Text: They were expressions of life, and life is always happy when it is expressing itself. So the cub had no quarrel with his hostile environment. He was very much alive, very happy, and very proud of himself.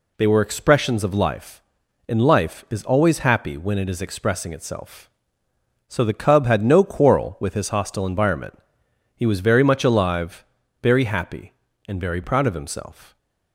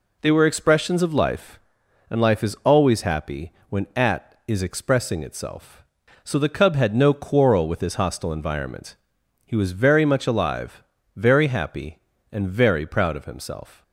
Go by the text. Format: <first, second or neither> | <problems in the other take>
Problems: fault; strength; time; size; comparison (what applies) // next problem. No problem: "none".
first | pauses between "happy" and "when"; slight; at 3.5 s; 0.16 s long // says "at" for "it"; at 3.9 s